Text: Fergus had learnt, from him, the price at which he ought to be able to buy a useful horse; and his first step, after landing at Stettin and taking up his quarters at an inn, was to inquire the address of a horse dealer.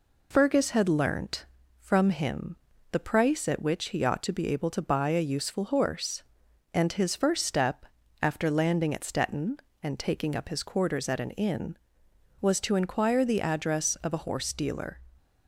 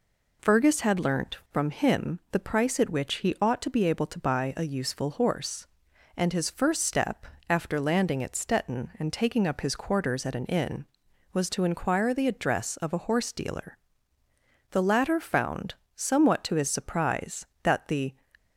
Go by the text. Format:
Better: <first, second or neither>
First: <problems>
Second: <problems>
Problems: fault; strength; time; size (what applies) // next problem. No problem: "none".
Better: first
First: none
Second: goes on to say "The latter found somewhat to his surprise that the"; strong; from 14.7 s on; 3.4 s long